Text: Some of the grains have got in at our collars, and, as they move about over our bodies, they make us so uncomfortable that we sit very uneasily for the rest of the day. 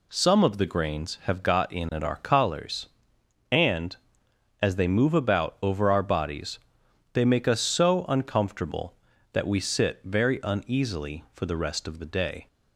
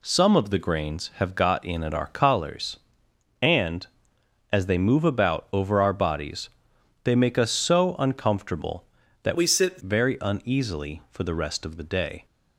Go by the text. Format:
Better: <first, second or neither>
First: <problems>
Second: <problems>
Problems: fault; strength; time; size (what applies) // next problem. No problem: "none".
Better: first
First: none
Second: changes voice from "we" to "sit"; from 9.3 to 9.8 s; 0.5 s long